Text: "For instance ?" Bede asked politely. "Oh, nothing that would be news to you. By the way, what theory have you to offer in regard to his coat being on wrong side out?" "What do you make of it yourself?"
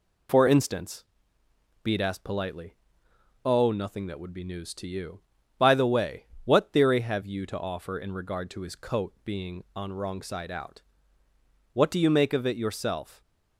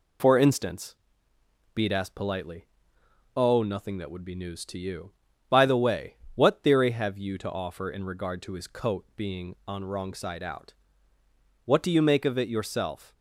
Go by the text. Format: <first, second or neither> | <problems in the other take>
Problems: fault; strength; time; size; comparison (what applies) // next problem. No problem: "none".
neither | none